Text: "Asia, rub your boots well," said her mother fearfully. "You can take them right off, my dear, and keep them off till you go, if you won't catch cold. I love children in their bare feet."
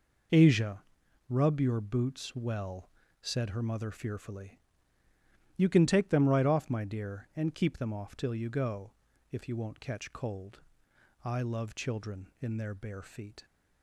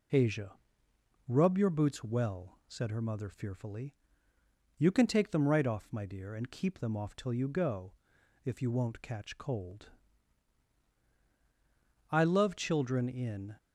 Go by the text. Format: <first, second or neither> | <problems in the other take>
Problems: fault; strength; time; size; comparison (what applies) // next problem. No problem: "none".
first | stops before "their bare feet"; at 13.5 s